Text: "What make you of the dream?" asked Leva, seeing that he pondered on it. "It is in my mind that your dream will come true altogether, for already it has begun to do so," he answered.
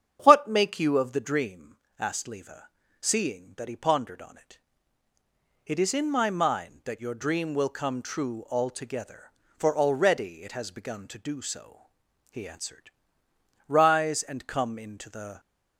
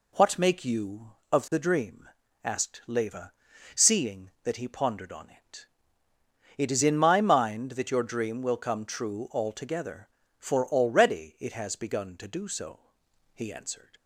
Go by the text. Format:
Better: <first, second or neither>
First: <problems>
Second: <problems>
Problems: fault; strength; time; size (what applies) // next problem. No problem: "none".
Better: second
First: starts louder than the rest; strong; until 1.2 s; 8.5 dB // goes on to say "Rise and come into the"; strong; from 13.6 s on; 1.7 s long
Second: none